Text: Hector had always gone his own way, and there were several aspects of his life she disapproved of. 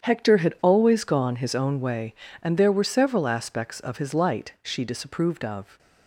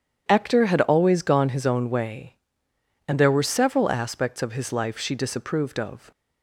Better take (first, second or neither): second